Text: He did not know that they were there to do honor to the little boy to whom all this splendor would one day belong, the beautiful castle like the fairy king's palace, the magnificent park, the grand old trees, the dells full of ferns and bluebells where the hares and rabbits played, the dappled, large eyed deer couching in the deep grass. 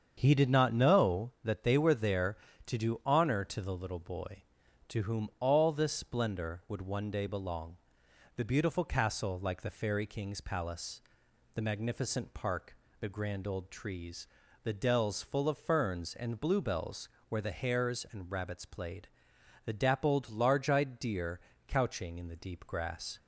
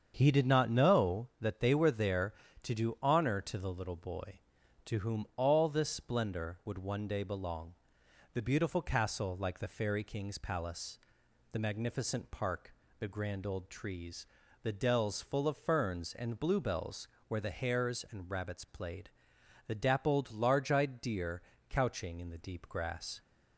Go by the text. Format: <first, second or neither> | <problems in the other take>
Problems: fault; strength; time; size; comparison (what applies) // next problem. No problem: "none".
neither | starts louder than the rest; strong; the same in both // pauses between "bluebells" and "where"; slight; the same in both // pauses between "deer" and "couching"; slight; the same in both